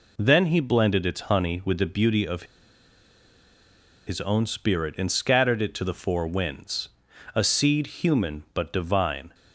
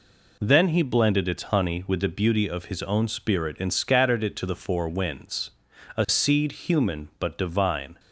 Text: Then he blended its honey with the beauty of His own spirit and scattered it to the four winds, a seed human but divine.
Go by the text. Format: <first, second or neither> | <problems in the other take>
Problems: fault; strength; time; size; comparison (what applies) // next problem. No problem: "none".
second | pauses between "of" and "His"; strong; at 2.4 s; 1.6 s long